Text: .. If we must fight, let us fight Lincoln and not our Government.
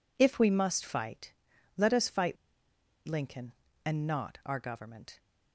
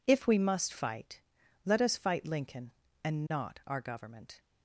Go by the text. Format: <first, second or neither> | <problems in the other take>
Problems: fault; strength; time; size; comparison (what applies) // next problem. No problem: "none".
second | pauses between "fight" and "Lincoln"; noticeable; at 2.3 s; 0.72 s long